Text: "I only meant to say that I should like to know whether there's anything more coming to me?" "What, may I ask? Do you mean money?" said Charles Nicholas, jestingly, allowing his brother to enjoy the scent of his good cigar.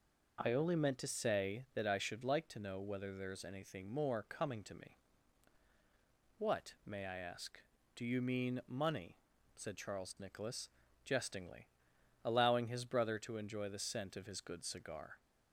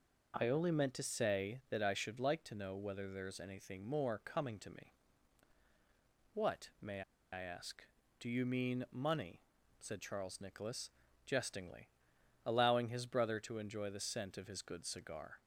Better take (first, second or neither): first